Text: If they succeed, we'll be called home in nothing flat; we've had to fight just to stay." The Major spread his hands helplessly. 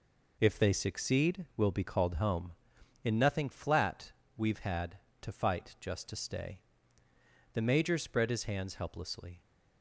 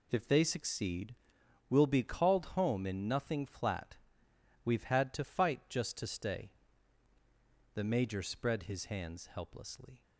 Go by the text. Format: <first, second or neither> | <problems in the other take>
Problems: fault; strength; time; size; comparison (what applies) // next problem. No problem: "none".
neither | none